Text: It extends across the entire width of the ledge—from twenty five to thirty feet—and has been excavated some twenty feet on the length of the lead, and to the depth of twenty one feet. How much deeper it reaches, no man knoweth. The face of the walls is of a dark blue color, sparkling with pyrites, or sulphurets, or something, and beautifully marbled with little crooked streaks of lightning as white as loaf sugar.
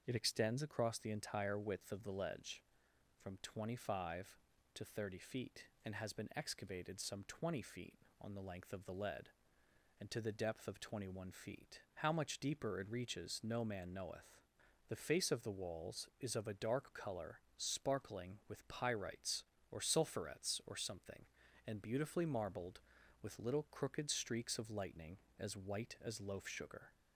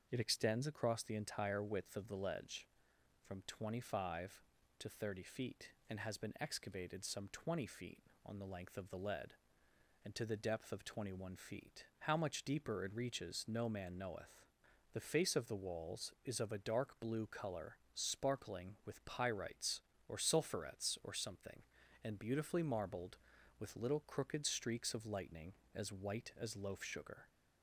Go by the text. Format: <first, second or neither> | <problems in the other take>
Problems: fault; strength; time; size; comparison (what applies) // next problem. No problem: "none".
second | starts louder than the rest; until 1.0 s; 6.5 dB; also in the second // skips "blue"; at 16.9 s